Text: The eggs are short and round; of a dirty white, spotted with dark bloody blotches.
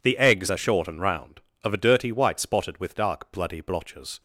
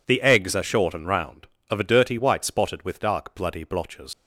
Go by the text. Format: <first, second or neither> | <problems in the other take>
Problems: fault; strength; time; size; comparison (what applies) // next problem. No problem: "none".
first | leaves "blotches" unfinished; at 4.1 s; 100 ms